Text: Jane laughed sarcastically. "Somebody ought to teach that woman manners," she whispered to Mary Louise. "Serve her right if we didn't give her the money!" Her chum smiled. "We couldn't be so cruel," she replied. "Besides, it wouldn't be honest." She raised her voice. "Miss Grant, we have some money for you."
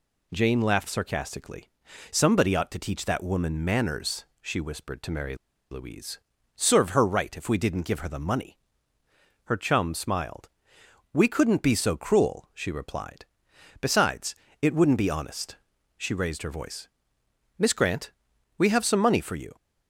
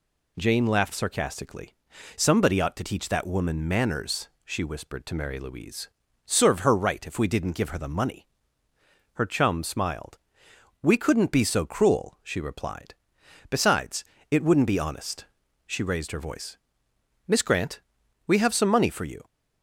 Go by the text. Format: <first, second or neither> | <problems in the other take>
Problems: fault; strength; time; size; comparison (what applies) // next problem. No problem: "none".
second | pauses between "Mary" and "Louise"; slight; at 5.3 s; 0.35 s long